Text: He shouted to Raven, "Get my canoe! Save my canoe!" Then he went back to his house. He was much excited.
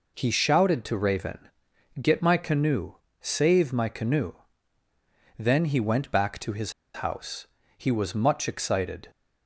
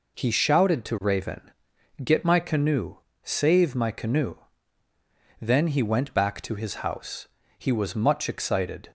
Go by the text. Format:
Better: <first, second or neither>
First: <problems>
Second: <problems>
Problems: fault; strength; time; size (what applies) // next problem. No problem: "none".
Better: second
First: pauses between "his" and "house"; slight; at 6.7 s; 0.32 s long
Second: none